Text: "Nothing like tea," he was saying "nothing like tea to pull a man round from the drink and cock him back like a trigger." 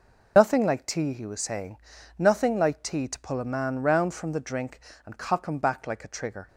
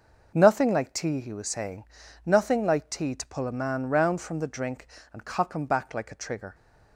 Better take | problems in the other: second | loses the start of "Nothing"; at 0.3 s; 85 ms // pauses between "saying" and "nothing"; at 1.7 s; 0.40 s long; also in the second

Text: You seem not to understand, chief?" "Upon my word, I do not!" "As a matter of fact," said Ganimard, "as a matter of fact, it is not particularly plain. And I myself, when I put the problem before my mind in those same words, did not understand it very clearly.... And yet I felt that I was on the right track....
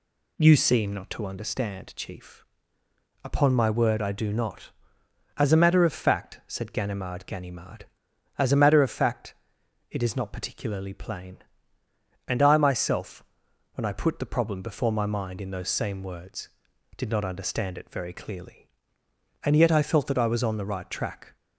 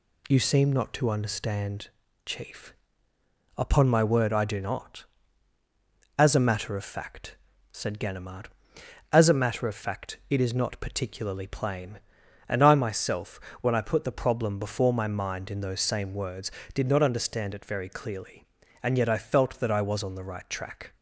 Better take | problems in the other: second | says "Ganimard" twice; at 7.2 s

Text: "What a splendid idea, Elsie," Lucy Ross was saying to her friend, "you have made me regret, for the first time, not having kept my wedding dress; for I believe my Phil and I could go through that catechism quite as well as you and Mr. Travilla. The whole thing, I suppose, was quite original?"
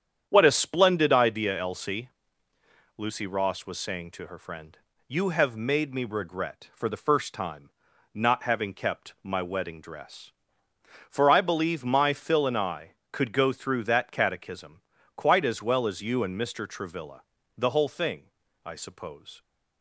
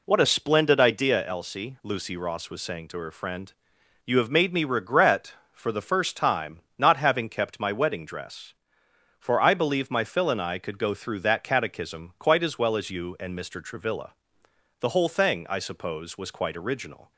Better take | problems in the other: second | starts louder than the rest; strong; until 1.3 s; 8.5 dB // pauses between "catechism" and "quite"; slight; at 14.8 s; 0.36 s long // stops before "was quite original"; at 19.4 s

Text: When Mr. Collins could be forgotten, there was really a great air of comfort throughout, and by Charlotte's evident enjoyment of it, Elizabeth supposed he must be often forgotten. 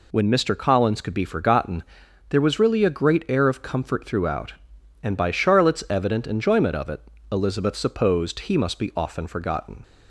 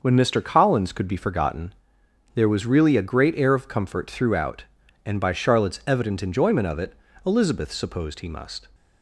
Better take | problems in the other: first | starts louder than the rest; noticeable; until 1.0 s; 6 dB // stops before "be often forgotten"; at 8.7 s

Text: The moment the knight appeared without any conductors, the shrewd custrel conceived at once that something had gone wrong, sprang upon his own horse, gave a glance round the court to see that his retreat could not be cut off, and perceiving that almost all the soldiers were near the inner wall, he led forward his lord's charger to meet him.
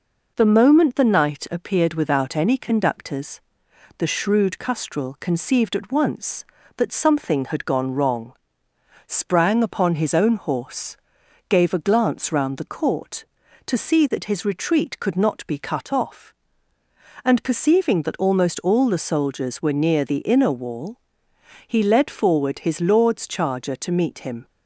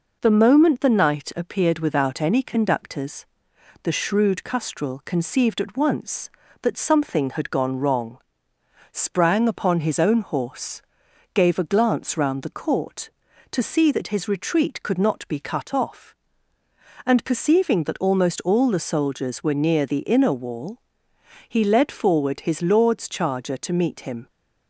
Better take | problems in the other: neither | none

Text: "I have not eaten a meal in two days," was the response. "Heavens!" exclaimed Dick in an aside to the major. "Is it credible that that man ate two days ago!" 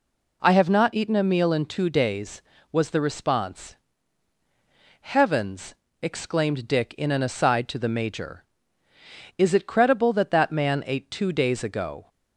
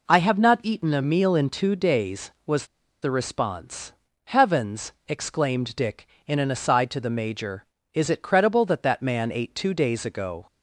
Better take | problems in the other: first | pauses between "was" and "the"; at 2.6 s; 0.36 s long

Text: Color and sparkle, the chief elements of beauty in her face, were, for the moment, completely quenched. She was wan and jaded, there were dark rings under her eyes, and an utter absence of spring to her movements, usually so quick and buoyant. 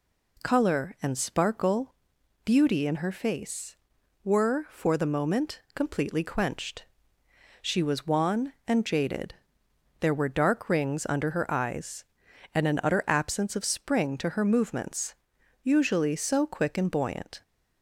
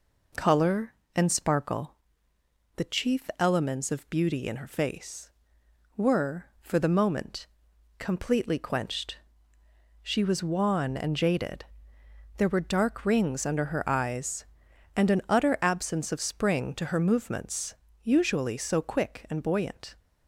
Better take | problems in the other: second | skips "the chief elements of"; at 2.1 s

